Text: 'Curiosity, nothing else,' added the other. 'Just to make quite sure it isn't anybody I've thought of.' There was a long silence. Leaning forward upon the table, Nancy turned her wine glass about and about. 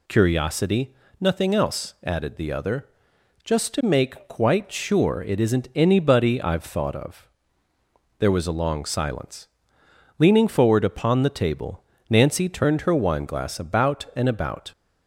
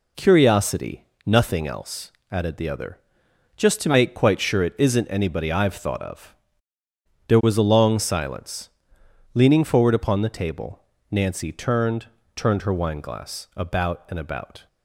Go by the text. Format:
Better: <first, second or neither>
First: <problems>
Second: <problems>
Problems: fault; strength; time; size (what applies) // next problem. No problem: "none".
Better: first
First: none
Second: says "turned" twice; at 12.3 s